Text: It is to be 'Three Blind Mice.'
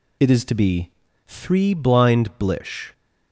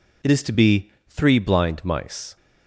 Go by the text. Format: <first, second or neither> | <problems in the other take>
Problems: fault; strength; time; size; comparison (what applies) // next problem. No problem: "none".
second | pauses between "be" and "Three"; at 0.9 s; 0.36 s long; slight in the second // says "Blish" for "Mice"; at 2.3 s